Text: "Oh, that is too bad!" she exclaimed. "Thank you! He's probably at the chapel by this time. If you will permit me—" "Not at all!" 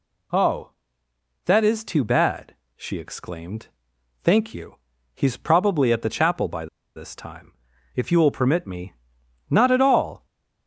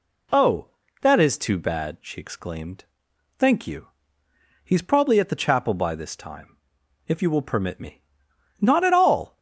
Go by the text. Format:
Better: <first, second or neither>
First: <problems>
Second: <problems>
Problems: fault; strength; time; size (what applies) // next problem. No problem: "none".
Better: second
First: pauses between "by" and "this"; slight; at 6.6 s; 0.30 s long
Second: none